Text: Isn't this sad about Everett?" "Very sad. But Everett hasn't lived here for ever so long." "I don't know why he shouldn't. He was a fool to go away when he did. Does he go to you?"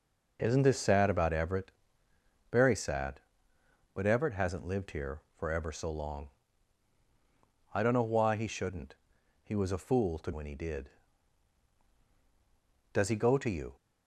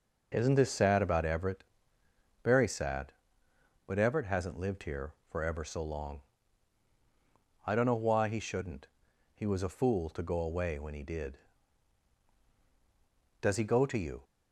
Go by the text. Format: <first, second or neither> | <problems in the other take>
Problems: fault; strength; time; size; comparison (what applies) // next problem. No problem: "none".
second | skips "go away"; at 10.3 s